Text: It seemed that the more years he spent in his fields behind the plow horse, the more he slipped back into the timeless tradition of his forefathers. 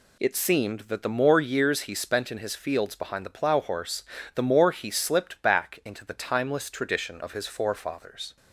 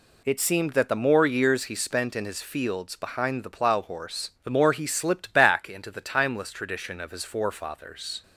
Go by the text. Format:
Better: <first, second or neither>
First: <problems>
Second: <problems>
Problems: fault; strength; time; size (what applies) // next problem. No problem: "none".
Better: neither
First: none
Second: none